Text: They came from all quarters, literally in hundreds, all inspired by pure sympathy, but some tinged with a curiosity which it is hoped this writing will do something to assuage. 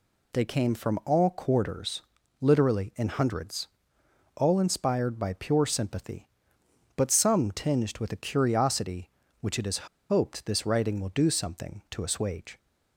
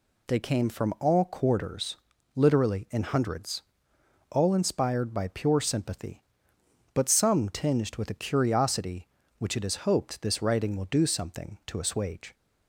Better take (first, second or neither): second